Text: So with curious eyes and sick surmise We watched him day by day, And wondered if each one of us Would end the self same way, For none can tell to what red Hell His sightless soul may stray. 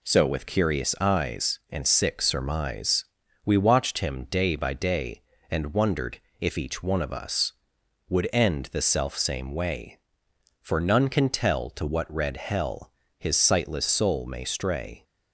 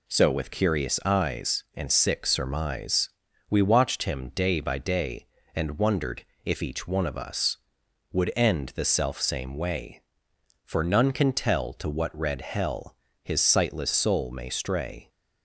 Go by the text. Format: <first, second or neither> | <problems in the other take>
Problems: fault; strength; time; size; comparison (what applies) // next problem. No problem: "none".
neither | pauses between "surmise" and "We"; the same in both // pauses between "wondered" and "if"; slight; the same in both // pauses between "Hell" and "His"; slight; the same in both